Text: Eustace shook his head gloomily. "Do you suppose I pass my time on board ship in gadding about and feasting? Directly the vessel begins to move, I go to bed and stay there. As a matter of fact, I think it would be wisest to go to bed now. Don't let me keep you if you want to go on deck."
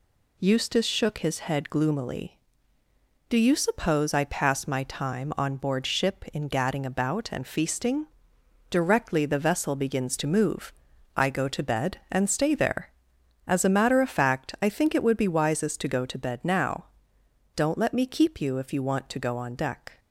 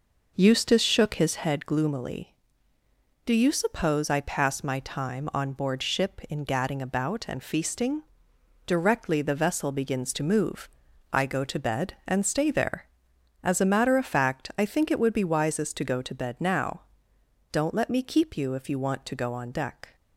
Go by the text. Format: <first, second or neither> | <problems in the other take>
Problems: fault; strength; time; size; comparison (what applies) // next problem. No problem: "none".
first | starts louder than the rest; noticeable; until 1.6 s; 5.5 dB